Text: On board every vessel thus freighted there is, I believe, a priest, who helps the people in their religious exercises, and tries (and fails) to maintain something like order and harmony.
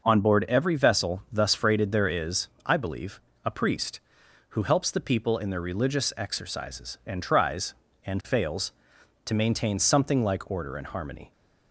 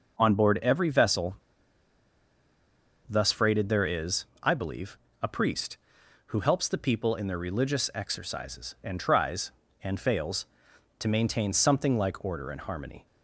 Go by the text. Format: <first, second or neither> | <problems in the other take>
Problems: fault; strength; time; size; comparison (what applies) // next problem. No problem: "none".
first | pauses between "vessel" and "thus"; strong; at 1.3 s; 1.7 s long